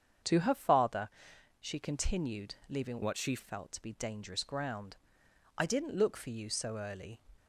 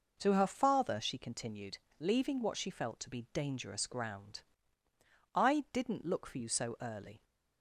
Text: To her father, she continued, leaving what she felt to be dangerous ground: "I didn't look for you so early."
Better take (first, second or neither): second